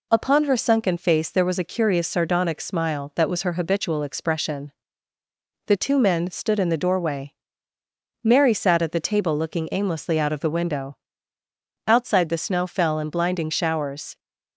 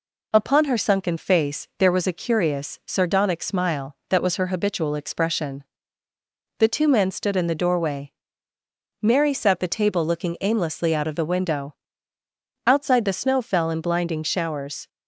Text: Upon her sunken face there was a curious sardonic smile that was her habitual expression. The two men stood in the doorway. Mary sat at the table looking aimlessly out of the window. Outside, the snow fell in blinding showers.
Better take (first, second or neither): first